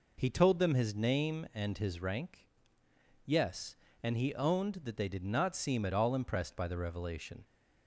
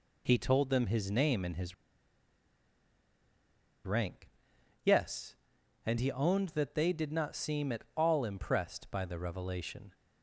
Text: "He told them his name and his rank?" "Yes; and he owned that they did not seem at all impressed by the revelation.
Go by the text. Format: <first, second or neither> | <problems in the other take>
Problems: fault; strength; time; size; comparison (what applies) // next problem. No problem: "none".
first | pauses between "his" and "rank"; strong; at 1.7 s; 2.1 s long